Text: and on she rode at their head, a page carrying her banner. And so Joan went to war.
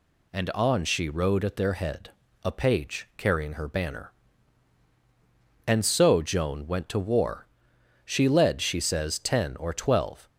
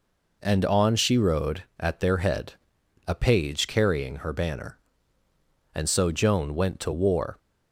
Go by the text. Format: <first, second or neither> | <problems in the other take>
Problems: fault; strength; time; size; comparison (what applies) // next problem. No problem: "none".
second | goes on to say "She led she says ten or twelve"; strong; from 8.0 s on; 2.2 s long